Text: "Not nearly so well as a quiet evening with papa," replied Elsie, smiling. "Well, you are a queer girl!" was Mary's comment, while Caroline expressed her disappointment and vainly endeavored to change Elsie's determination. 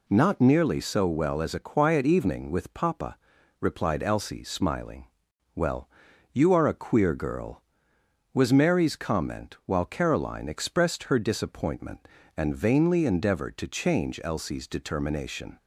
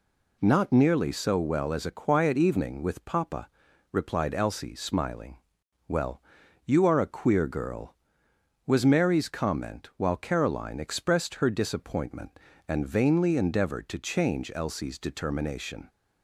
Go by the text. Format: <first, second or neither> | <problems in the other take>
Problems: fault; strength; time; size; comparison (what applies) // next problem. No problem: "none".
neither | none